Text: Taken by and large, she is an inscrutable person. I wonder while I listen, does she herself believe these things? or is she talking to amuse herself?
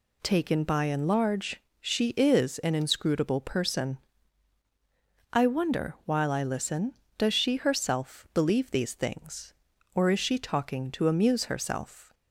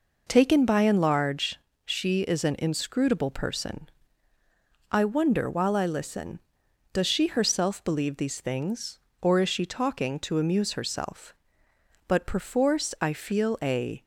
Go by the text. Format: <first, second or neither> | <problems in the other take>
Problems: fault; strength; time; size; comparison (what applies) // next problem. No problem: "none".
first | goes on to say "But perforce I feel a"; strong; from 12.0 s on; 1.9 s long